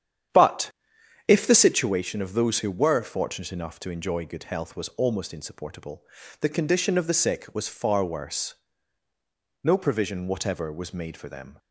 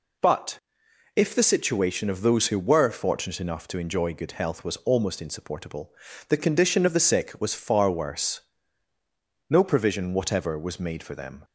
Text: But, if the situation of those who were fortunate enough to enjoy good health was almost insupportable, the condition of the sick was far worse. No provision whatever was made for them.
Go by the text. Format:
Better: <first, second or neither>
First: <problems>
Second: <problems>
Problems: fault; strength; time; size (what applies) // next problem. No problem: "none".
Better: second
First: starts louder than the rest; strong; until 1.9 s; 9.5 dB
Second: none